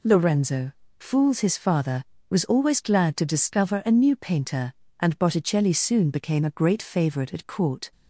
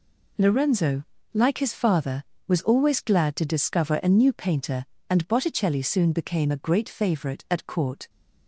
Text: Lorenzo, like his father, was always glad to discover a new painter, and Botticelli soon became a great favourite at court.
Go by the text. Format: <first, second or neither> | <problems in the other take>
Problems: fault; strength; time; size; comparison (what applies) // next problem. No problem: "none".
second | says "fools" for "like"; at 0.9 s